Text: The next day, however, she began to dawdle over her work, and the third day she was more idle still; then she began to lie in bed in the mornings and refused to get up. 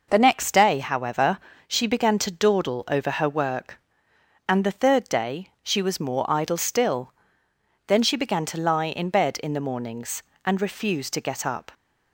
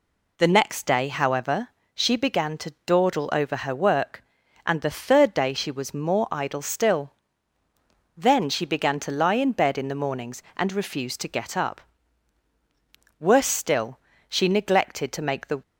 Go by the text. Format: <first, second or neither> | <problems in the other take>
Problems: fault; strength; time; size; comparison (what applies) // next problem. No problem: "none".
first | goes on to say "Worse still she neglected to make the"; strong; from 13.1 s on; 2.4 s long